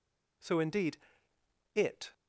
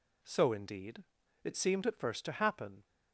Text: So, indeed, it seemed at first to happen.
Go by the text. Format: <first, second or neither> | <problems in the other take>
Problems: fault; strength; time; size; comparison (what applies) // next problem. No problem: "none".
second | stops before "seemed at first to happen"; at 2.1 s